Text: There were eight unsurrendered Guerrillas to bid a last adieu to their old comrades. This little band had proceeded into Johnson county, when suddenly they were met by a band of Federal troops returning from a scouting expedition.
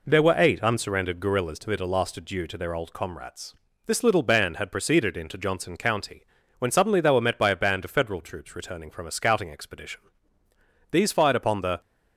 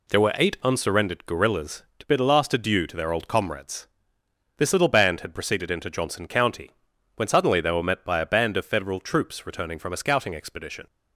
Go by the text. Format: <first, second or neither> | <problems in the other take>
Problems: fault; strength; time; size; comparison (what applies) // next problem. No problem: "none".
second | goes on to say "These fired upon the"; noticeable; from 10.9 s on; 0.90 s long